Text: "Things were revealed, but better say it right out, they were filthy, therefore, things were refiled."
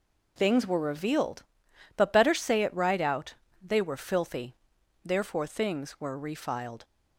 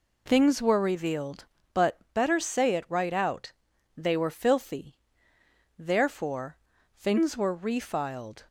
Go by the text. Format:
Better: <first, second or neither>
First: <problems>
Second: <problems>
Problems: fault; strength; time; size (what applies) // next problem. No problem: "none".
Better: neither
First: none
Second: none